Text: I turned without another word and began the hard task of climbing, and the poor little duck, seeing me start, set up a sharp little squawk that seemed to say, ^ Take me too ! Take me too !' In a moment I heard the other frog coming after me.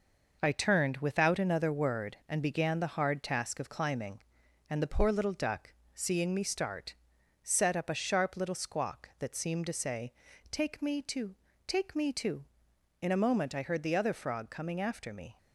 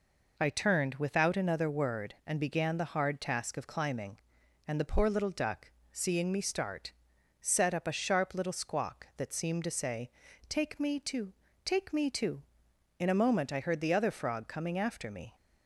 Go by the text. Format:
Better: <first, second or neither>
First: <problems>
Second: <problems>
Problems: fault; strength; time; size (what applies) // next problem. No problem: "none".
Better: second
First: gets quieter; strong; throughout; 8.5 dB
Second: none